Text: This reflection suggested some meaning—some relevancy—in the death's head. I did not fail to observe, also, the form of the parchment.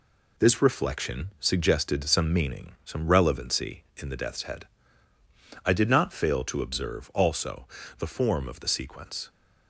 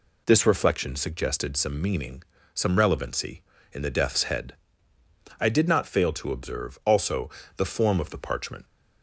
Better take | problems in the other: second | says "sequence" for "parchment"; at 8.6 s

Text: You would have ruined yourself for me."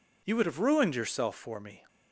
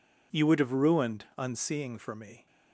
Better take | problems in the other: first | says "unseeing" for "yourself"; at 1.3 s

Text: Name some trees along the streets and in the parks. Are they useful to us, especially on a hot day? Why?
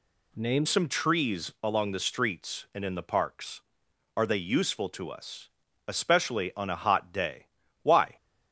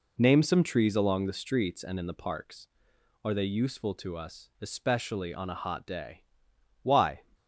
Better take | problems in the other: second | changes voice at "some"; from 0.6 s on; 7.4 s long

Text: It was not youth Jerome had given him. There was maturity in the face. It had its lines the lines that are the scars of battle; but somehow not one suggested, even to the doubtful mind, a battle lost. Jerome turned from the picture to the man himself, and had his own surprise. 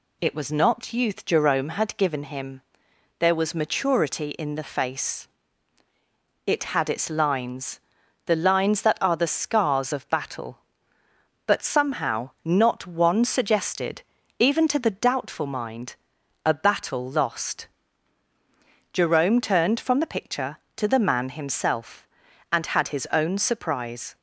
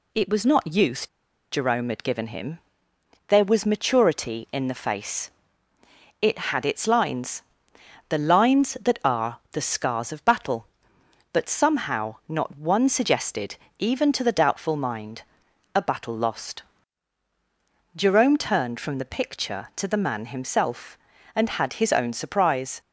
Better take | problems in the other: first | pauses between "youth" and "Jerome"; at 1.0 s; 0.44 s long // pauses between "lines" and "the"; noticeable; at 7.4 s; 0.68 s long; noticeable in the first

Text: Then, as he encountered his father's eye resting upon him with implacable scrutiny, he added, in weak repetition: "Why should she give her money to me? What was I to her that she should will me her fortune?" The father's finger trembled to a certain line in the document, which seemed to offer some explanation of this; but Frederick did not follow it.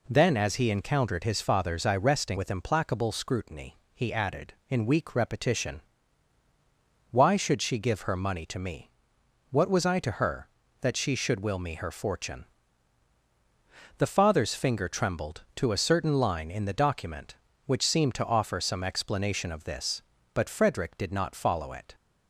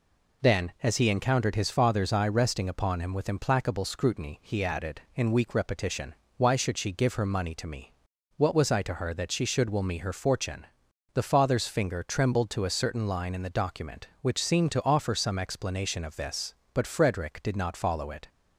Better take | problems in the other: second | skips "upon him"; at 2.3 s

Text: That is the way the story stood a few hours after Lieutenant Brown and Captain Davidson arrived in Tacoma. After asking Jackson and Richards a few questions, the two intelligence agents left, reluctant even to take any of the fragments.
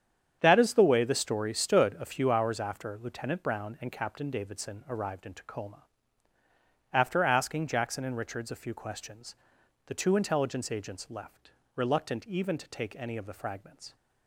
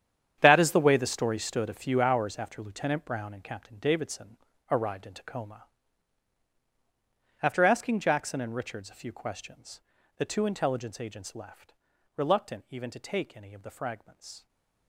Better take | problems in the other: first | gets quieter; strong; throughout; 13.5 dB // starts louder than the rest; strong; until 1.4 s; 9 dB; strong in the first // pauses between "Davidson" and "arrived"; slight; at 4.3 s; 0.34 s long // stays silent after the last word; slight; from 14.3 s on; 0.5 s long

